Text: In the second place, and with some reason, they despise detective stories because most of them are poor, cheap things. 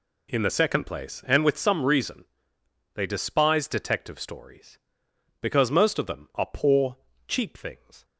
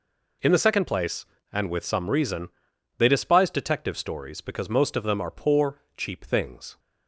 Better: neither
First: none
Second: none

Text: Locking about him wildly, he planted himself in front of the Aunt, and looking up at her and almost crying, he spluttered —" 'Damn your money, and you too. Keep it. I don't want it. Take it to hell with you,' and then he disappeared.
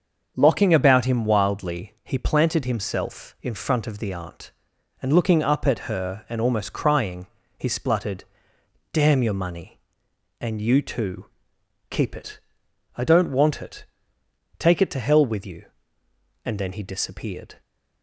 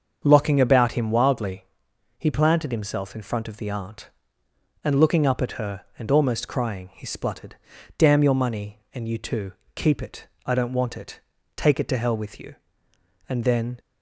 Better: first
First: starts louder than the rest; until 1.3 s; 7 dB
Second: starts louder than the rest; until 1.2 s; 7 dB // stops before "he disappeared"; at 13.7 s

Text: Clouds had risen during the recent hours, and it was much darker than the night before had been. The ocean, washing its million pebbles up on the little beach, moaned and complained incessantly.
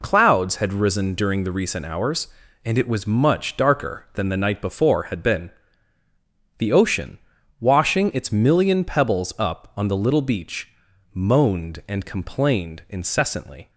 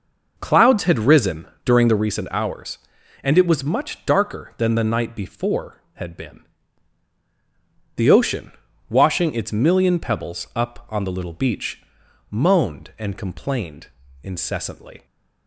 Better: first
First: none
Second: starts louder than the rest; noticeable; until 2.2 s; 5.5 dB // pauses between "risen" and "during"; slight; at 1.4 s; 0.18 s long // pauses between "complained" and "incessantly"; slight; at 13.8 s; 0.36 s long

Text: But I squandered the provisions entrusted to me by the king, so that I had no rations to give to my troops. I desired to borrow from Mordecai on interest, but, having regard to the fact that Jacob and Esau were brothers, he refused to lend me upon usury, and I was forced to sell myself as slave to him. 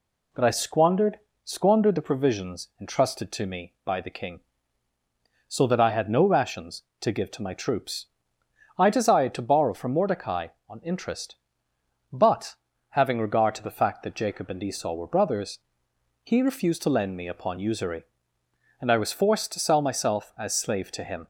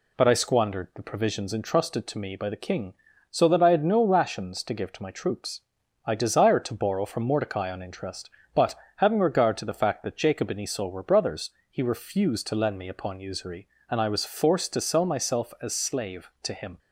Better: second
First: says "squandered" twice; at 1.4 s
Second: none

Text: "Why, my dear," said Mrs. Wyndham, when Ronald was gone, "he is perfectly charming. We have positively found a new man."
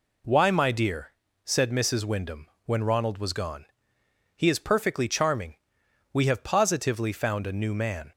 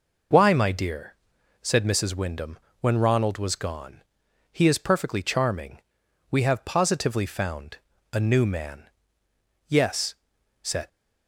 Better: first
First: none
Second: pauses between "found" and "a"; at 7.7 s; 0.38 s long // goes on to say "Yes said"; noticeable; from 9.6 s on; 1.2 s long

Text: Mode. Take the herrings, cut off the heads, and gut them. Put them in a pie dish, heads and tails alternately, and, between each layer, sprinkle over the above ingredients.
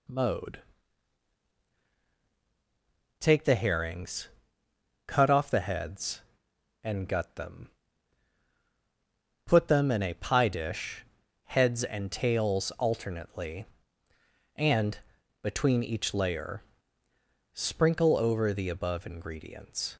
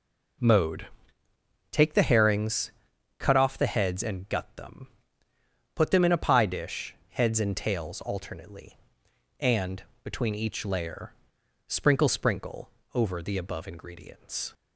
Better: first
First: none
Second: says "sprinkle" twice; at 12.0 s

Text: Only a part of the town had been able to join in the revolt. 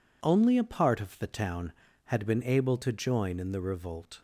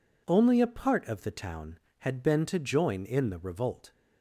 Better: first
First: none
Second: skips "able"; at 2.4 s

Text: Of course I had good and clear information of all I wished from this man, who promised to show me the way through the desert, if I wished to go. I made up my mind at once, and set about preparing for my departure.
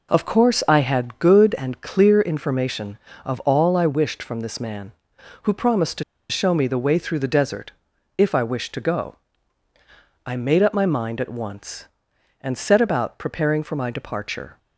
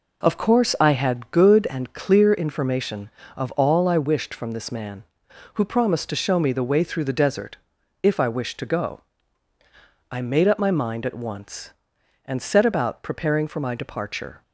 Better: second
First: pauses between "to" and "show"; slight; at 6.0 s; 0.26 s long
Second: none

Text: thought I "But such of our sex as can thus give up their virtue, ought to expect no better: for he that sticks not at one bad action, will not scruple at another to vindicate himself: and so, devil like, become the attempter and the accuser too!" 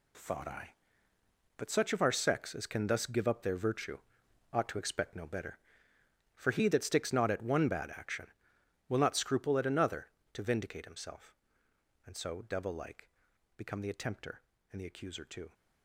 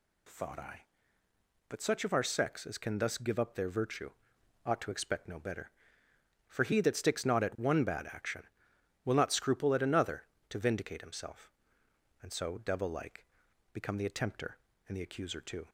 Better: second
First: gets quieter; strong; throughout; 10 dB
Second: none

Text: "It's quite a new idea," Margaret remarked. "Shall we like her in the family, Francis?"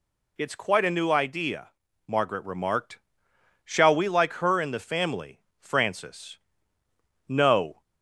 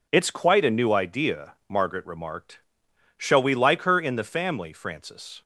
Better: second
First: goes on to say "No"; from 7.2 s on; 0.54 s long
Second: none

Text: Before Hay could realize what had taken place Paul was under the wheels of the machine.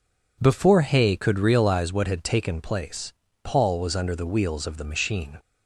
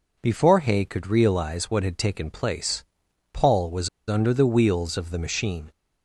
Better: first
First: pauses between "place" and "Paul"; slight; at 3.1 s; 0.32 s long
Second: pauses between "place" and "Paul"; noticeable; at 2.8 s; 0.50 s long // pauses between "was" and "under"; slight; at 3.8 s; 0.20 s long

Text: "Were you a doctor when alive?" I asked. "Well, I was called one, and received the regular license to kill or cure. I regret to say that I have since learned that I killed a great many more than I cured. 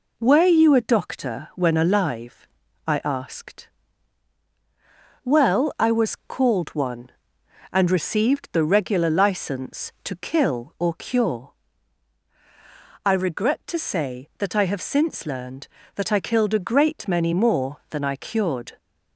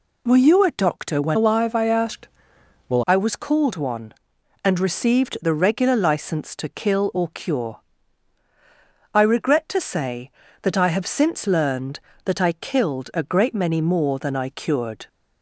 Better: first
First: none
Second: changes voice from "alive" to "Well"; from 1.3 to 3.0 s; 1.7 s long

